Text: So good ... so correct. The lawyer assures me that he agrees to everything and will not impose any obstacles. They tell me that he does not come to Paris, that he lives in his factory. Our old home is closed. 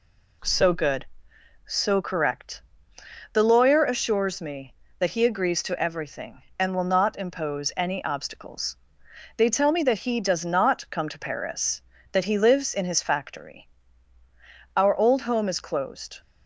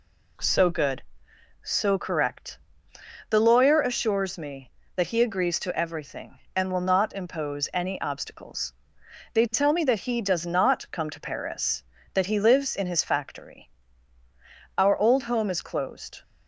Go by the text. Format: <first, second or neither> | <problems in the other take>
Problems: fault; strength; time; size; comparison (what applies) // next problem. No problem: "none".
neither | none